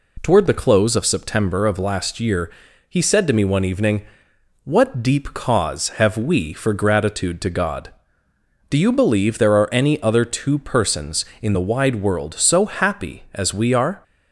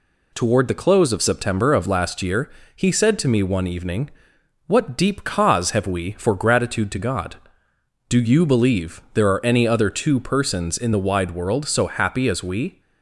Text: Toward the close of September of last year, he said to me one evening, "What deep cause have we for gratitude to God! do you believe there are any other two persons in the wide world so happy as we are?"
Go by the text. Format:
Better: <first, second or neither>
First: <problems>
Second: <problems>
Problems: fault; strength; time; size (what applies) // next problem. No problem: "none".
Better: first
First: none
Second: stops before "are"; at 12.8 s